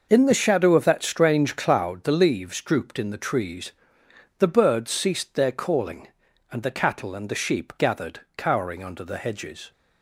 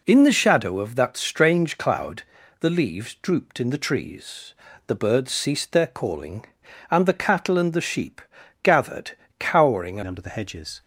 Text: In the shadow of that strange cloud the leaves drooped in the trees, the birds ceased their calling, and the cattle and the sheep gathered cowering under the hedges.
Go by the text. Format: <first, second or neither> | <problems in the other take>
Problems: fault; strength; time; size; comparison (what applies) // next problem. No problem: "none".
first | pauses between "cloud" and "the"; slight; at 2.2 s; 0.36 s long // pauses between "sheep" and "gathered"; at 8.1 s; 0.44 s long // pauses between "gathered" and "cowering"; slight; at 9.1 s; 0.28 s long; slight in the first // changes voice at "under"; from 10.0 s on; 0.8 s long